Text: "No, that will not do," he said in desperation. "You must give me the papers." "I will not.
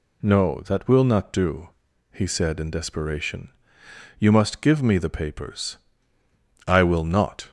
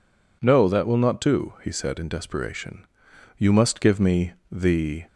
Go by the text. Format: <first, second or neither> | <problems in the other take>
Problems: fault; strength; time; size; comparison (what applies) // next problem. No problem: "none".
first | pauses between "me" and "the"; slight; at 4.3 s; 0.18 s long // stops before "papers I will not"; at 5.0 s